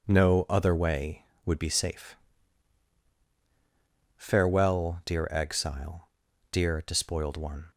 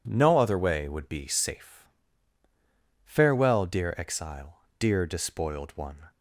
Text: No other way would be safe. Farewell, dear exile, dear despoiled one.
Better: neither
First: none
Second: none

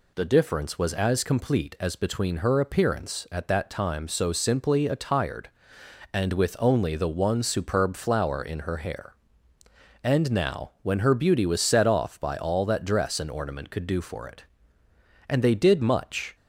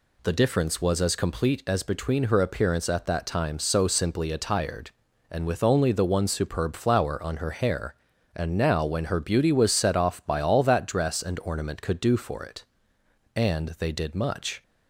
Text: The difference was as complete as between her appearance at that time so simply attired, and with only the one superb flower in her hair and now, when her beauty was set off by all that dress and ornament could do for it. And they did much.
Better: first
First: none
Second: says "on" for "in"; at 7.2 s

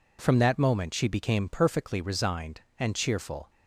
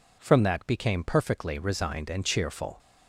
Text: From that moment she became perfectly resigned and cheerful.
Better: first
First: none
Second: skips "moment she"; at 0.6 s

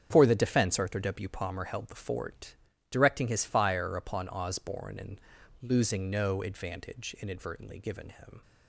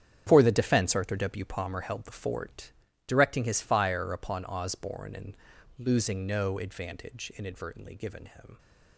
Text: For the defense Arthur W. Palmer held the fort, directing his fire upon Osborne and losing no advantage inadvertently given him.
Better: first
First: starts louder than the rest; strong; until 1.1 s; 8 dB // pauses between "and" and "losing"; at 5.2 s; 0.40 s long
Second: gets quieter; strong; throughout; 12.5 dB // starts louder than the rest; strong; until 1.2 s; 9 dB // pauses between "and" and "losing"; at 5.3 s; 0.40 s long

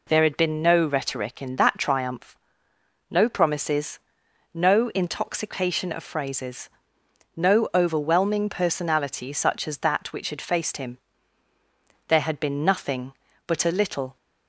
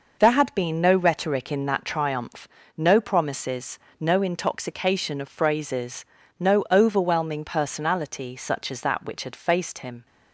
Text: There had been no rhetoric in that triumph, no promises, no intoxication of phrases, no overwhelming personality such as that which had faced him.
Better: second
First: goes on to say "There had been nothing but a little"; strong; from 12.0 s on; 2.0 s long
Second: none

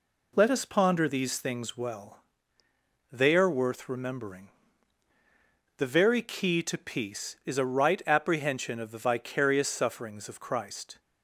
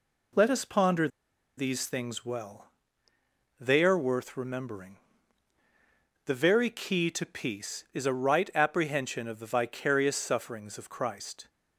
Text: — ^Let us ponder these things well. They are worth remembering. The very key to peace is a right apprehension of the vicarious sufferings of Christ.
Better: first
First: none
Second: pauses between "ponder" and "these"; noticeable; at 1.0 s; 0.49 s long

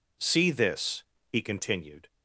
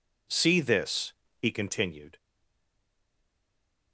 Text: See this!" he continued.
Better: first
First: none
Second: stays silent after the last word; noticeable; from 2.1 s on; 1.8 s long

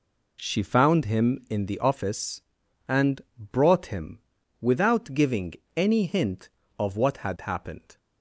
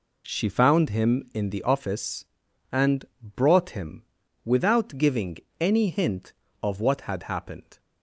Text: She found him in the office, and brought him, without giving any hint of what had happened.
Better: neither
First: pauses between "and" and "brought"; slight; at 3.1 s; 0.18 s long // pauses between "giving" and "any"; slight; at 5.5 s; 0.20 s long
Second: pauses between "and" and "brought"; slight; at 3.0 s; 0.18 s long // pauses between "giving" and "any"; slight; at 5.3 s; 0.20 s long

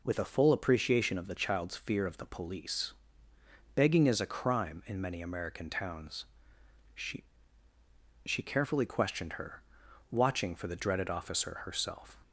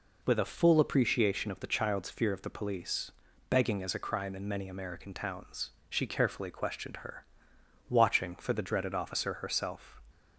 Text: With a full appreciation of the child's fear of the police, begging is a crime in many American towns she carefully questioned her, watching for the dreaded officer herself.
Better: second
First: pauses between "towns" and "she"; noticeable; at 6.2 s; 0.70 s long // says "she" twice; at 8.2 s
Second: pauses between "towns" and "she"; slight; at 5.7 s; 0.18 s long

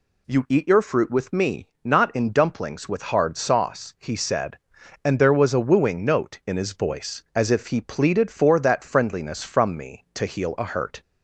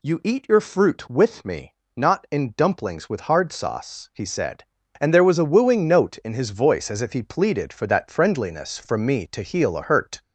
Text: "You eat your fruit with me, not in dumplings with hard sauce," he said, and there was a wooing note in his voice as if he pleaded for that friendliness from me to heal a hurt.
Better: neither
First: none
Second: none

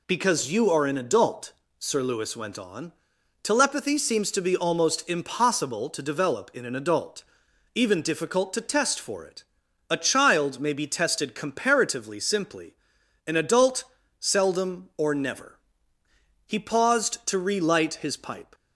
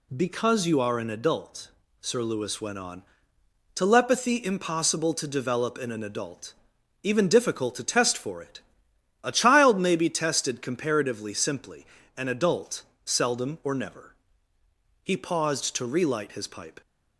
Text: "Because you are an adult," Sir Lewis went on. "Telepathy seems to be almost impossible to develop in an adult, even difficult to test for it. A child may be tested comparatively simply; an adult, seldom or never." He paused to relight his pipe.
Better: first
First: none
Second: skips "seems to be almost"; at 4.4 s

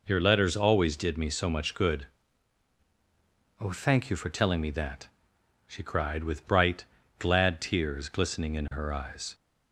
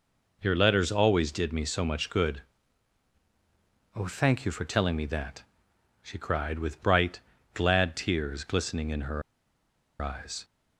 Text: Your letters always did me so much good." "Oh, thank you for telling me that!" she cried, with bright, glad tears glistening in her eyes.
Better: first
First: none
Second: pauses between "her" and "eyes"; noticeable; at 9.2 s; 0.80 s long

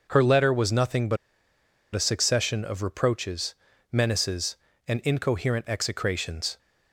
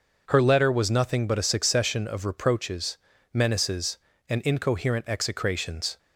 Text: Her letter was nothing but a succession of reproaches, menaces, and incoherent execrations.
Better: second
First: pauses between "but" and "a"; noticeable; at 1.1 s; 0.77 s long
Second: none

